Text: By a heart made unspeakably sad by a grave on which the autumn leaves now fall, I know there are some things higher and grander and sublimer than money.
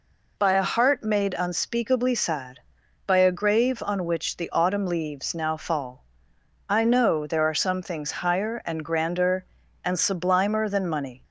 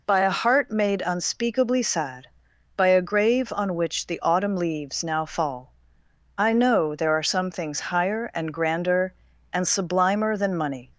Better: neither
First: none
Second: none

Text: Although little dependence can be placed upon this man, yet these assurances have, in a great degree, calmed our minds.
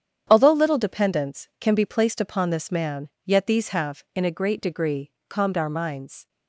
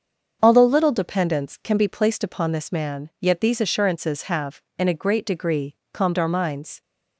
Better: second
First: starts louder than the rest; strong; until 1.3 s; 9 dB // skips "assurances"; at 3.6 s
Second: starts louder than the rest; until 1.4 s; 7 dB

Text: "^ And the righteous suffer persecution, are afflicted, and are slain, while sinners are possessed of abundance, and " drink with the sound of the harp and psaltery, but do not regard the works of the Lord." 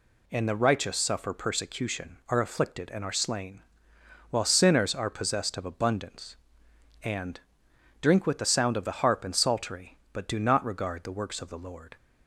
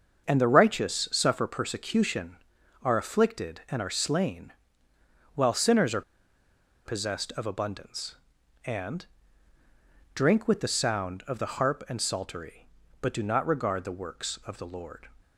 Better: first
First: none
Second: starts louder than the rest; until 1.2 s; 7 dB // pauses between "are" and "possessed"; noticeable; at 6.0 s; 0.84 s long

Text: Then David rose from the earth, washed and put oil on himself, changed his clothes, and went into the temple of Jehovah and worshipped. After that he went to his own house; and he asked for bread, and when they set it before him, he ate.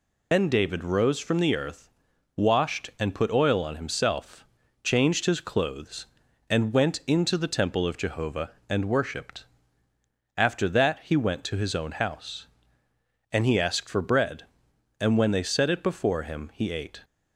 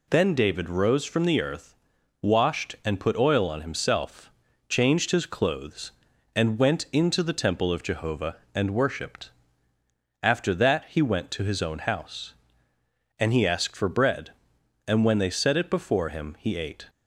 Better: second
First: loses the start of "Then"; at 0.3 s; 75 ms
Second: none

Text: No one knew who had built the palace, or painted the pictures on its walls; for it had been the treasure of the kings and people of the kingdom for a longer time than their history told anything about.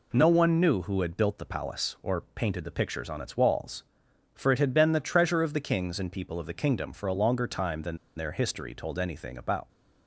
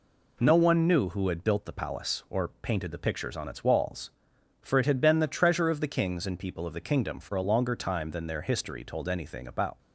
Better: second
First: pauses between "than" and "their"; slight; at 7.9 s; 0.20 s long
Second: none

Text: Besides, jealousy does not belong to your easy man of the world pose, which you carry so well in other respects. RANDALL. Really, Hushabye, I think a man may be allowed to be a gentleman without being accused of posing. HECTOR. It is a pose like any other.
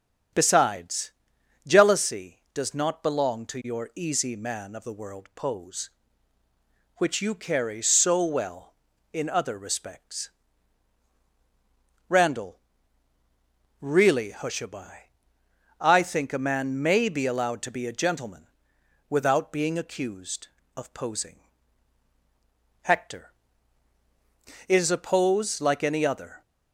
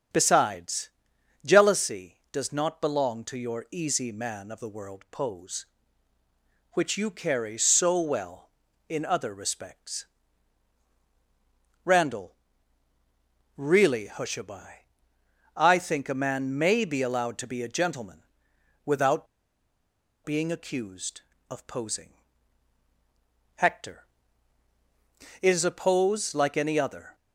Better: first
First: starts louder than the rest; strong; until 1.9 s; 7.5 dB // pauses between "gentleman" and "without"; noticeable; at 18.4 s; 0.62 s long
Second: starts louder than the rest; strong; until 1.6 s; 7.5 dB // pauses between "gentleman" and "without"; noticeable; at 18.2 s; 0.62 s long // pauses between "without" and "being"; at 19.2 s; 0.98 s long

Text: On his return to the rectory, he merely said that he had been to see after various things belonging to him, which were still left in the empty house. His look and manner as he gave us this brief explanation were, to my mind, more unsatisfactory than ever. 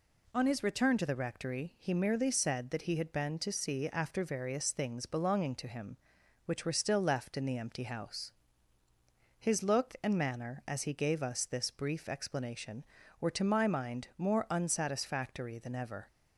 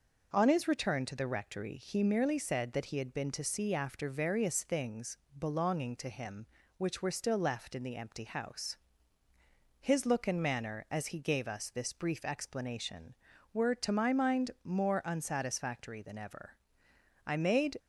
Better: first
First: none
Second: pauses between "things" and "belonging"; slight; at 5.1 s; 0.20 s long // goes on to say "I made"; from 17.2 s on; 0.52 s long

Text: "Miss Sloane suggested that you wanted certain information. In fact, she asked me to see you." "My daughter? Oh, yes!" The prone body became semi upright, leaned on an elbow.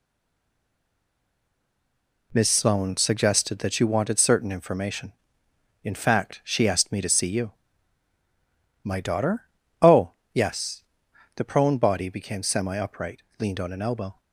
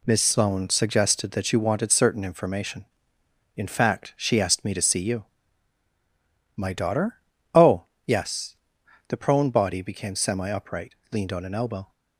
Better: second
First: stays silent before the first word; until 2.3 s; 2.3 s long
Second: none

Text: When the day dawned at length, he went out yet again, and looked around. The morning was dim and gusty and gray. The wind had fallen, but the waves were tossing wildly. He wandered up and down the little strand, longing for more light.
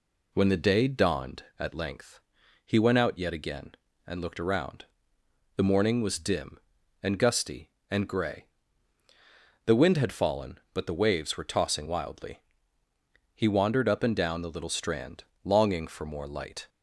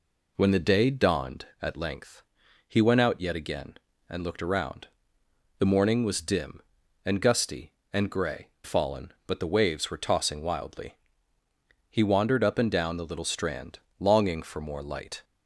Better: first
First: none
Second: skips "The wind had"; at 8.5 s

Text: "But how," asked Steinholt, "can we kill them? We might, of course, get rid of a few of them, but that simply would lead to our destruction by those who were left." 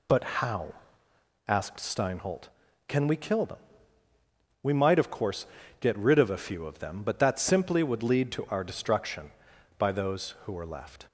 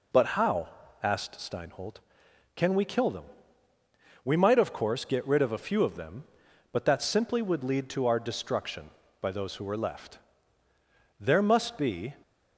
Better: first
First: none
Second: goes on to say "There must be"; noticeable; from 11.1 s on; 0.94 s long

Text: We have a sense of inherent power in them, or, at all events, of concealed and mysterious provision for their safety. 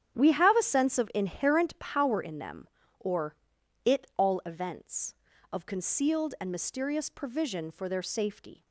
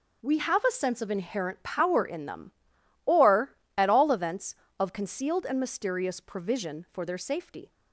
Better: second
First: starts louder than the rest; strong; until 1.2 s; 9.5 dB // says "it" for "at"; at 3.8 s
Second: none

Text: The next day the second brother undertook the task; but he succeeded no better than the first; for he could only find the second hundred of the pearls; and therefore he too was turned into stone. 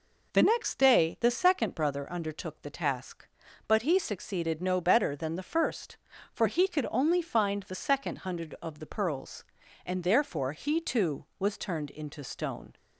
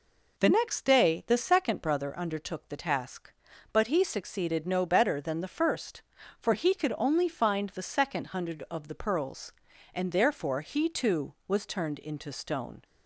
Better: neither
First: none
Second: none

